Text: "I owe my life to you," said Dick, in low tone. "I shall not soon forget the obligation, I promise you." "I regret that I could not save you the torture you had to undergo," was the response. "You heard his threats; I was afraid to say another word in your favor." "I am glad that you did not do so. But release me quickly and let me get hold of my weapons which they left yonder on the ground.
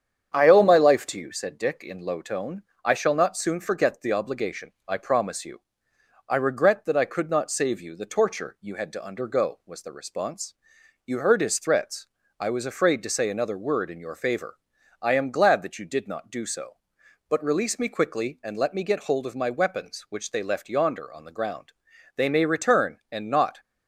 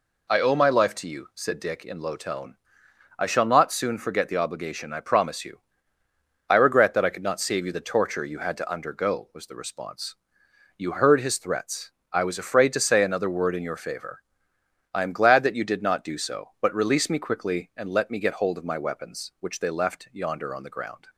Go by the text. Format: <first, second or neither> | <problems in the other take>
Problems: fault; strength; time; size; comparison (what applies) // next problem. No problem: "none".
second | starts louder than the rest; strong; until 1.3 s; 8 dB // goes on to say "They may return and not"; from 22.1 s on; 1.4 s long